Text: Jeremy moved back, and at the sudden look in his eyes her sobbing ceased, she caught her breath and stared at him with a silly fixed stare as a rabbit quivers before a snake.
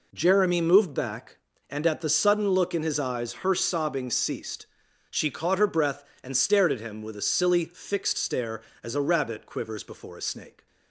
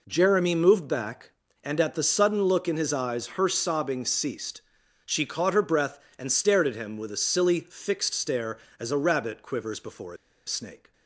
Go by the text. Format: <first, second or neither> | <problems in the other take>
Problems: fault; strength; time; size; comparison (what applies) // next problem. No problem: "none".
first | pauses between "a" and "snake"; slight; at 10.1 s; 0.31 s long